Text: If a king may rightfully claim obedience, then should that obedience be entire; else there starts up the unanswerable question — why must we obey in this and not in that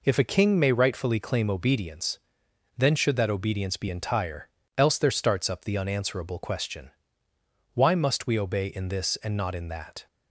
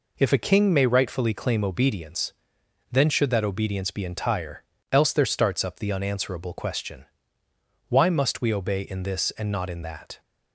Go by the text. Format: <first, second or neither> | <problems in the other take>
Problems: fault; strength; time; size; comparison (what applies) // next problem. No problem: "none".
neither | none